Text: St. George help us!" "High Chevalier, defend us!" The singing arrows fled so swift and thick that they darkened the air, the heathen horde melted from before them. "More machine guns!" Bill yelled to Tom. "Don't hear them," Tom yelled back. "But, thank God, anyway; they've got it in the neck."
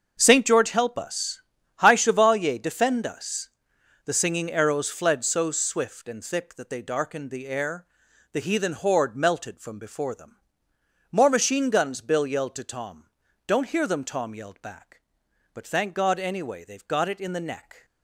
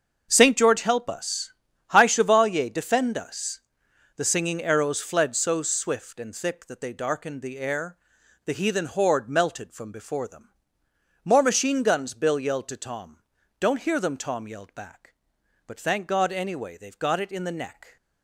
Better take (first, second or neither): neither